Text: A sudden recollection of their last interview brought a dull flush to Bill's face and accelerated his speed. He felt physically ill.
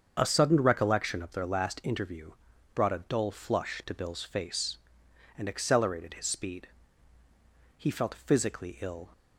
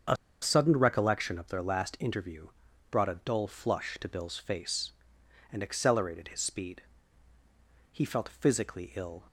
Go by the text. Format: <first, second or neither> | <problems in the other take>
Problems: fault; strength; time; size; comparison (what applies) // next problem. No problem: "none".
first | starts louder than the rest; until 1.3 s; 7 dB; also in the first // pauses between "A" and "sudden"; slight; at 0.1 s; 0.26 s long // pauses between "interview" and "brought"; at 2.4 s; 0.42 s long; also in the first